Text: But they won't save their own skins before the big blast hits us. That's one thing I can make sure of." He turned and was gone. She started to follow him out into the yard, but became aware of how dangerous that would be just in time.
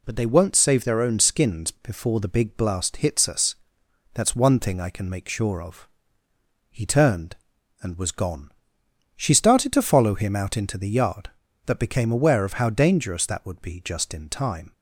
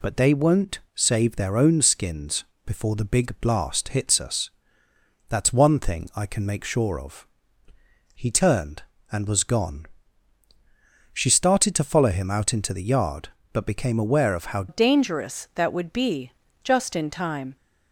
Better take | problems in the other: first | pauses between "won't" and "save"; slight; at 0.7 s; 0.16 s long // pauses between "skins" and "before"; slight; at 2.4 s; 0.22 s long // changes voice at "dangerous"; from 14.6 s on; 2.9 s long // pauses between "be" and "just"; slight; at 16.3 s; 0.30 s long

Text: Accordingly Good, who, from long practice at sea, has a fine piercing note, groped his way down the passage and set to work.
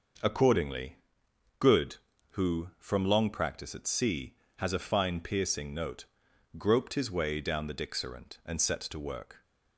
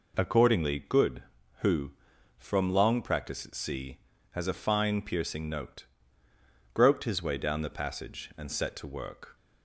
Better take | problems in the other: second | pauses between "Accordingly" and "Good"; noticeable; at 0.9 s; 0.62 s long // says "dixerant" for "passage"; at 7.7 s

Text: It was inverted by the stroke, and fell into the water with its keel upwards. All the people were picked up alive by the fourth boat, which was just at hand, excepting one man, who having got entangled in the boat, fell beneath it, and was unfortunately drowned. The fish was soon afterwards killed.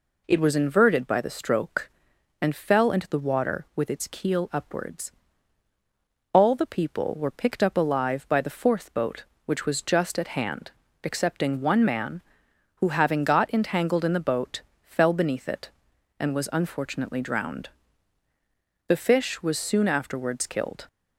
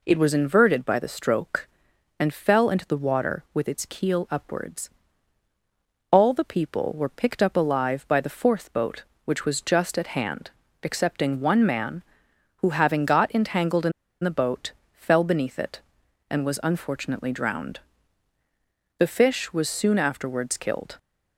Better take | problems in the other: first | pauses between "in" and "the"; slight; at 13.9 s; 0.31 s long

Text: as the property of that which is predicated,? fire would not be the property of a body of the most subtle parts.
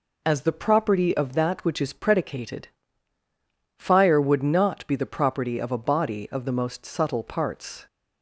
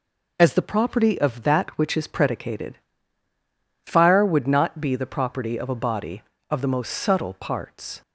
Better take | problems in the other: neither | none

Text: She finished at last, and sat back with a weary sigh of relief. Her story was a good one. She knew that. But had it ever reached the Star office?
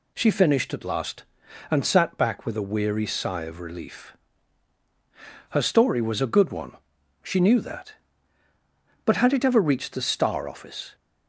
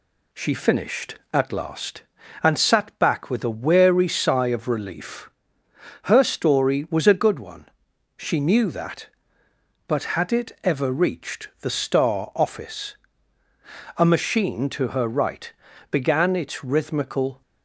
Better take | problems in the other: first | goes on to say "A machine to her right began its rhythmical"; strong; from 13.9 s on; 3.4 s long

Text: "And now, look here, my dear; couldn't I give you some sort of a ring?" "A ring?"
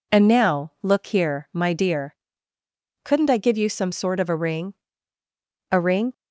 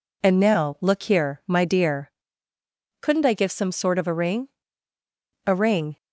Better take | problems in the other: first | skips "you"; at 3.5 s

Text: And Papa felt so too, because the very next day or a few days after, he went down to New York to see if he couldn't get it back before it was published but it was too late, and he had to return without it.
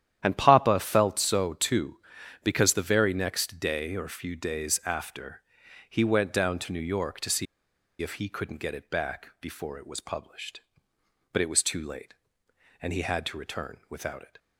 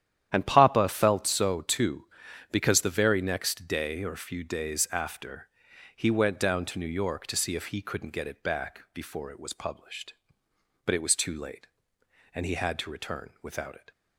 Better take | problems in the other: second | starts louder than the rest; strong; until 1.2 s; 10.5 dB; strong in the second // pauses between "see" and "if"; noticeable; at 7.4 s; 0.56 s long

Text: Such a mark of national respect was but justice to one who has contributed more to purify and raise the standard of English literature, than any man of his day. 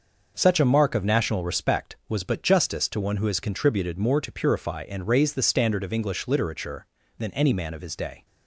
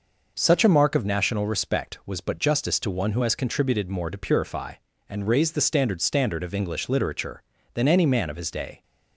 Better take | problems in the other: first | says "standard" twice; at 6.0 s

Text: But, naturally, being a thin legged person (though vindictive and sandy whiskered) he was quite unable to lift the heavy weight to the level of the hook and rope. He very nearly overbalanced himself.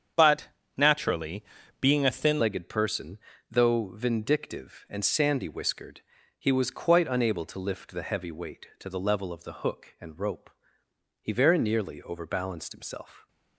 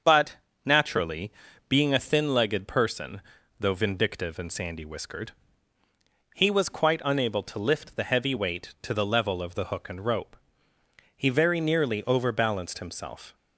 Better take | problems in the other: second | starts louder than the rest; strong; until 1.8 s; 7.5 dB; also in the second // changes voice at "legged"; from 2.3 s on; 10.9 s long

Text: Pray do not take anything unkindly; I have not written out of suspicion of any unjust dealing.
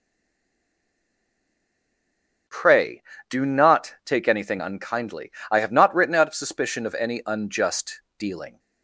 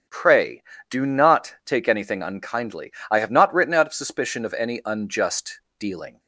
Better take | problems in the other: second | stays silent before the first word; until 2.4 s; 2.4 s long // starts louder than the rest; strong; until 3.7 s; 8 dB; strong in the second // pauses between "unjust" and "dealing"; slight; at 8.0 s; 0.16 s long; slight in the second

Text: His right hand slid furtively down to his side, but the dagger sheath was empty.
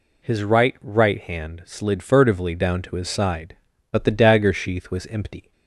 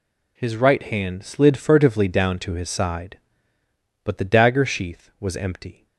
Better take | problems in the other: second | says "right" twice; at 0.8 s

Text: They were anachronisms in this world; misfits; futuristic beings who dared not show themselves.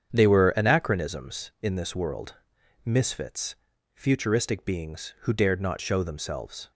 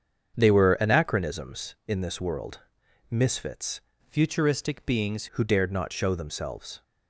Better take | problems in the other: first | starts louder than the rest; strong; until 1.4 s; 7.5 dB; strong in the first // changes voice from "futuristic" to "beings"; from 4.0 to 5.2 s; 1.2 s long

